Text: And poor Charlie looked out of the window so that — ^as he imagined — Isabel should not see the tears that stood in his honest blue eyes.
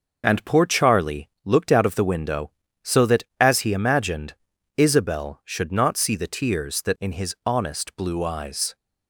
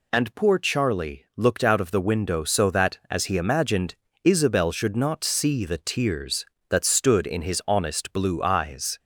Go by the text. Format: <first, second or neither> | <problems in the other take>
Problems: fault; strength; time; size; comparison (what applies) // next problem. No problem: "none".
second | pauses between "Charlie" and "looked"; slight; at 1.2 s; 0.16 s long // skips "stood"; at 6.9 s